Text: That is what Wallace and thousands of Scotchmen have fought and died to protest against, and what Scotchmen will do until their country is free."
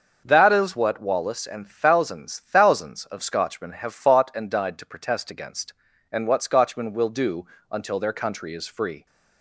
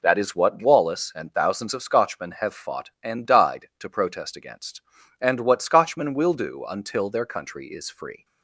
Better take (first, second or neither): second